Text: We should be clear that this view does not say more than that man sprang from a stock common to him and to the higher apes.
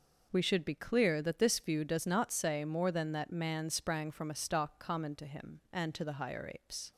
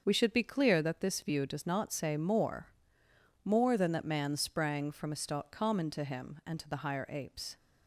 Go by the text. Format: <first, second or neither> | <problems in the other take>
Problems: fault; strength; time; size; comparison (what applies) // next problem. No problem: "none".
first | starts louder than the rest; until 1.0 s; 6.5 dB // says "more" twice; at 3.4 s